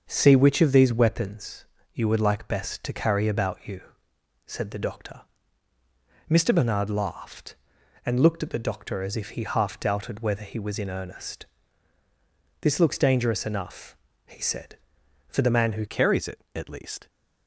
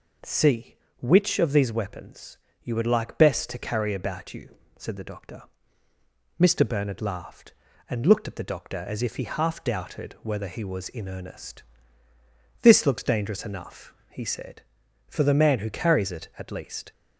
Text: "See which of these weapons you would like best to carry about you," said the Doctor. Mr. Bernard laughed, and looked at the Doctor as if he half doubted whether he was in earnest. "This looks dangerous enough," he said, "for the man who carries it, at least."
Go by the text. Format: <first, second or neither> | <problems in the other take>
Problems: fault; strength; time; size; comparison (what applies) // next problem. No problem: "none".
second | starts louder than the rest; until 1.1 s; 6.5 dB // pauses between "weapons" and "you"; slight; at 1.6 s; 0.28 s long; slight in the second // changes voice at "carries"; from 15.8 s on; 1.2 s long